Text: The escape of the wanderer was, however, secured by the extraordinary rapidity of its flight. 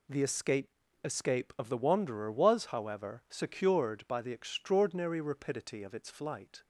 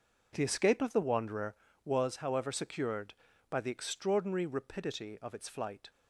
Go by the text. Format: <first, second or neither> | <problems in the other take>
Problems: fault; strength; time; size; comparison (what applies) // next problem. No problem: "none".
second | says "escape" twice; at 1.0 s